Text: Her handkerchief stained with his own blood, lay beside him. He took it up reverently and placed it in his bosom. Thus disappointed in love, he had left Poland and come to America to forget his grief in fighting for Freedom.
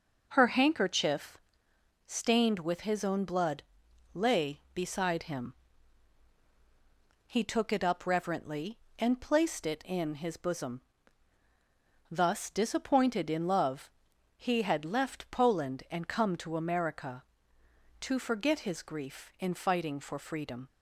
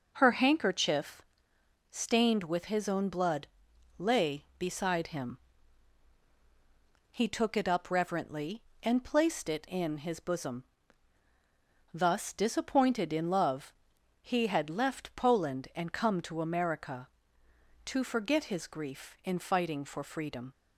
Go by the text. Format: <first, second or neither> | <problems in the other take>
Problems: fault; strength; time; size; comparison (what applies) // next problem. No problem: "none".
neither | pauses between "handkerchief" and "stained"; noticeable; the same in both